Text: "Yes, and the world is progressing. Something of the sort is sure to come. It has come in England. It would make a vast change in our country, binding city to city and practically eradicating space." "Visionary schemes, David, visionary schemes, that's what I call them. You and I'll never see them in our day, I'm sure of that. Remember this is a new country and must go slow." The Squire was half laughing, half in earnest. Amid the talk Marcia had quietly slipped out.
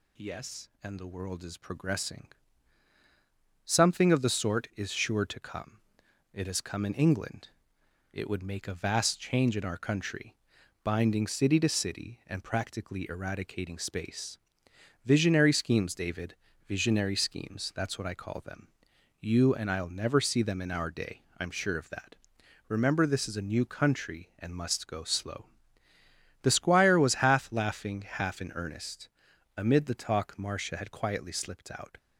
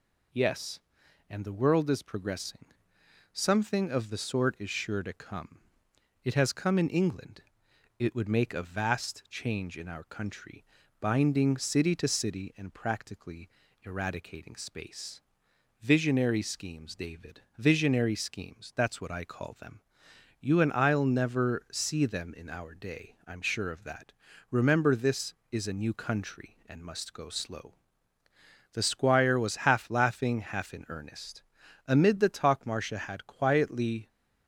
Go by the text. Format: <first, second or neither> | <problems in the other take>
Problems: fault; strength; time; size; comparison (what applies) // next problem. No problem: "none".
first | pauses between "practically" and "eradicating"; slight; at 13.4 s; 0.34 s long // stops before "slipped out"; at 34.0 s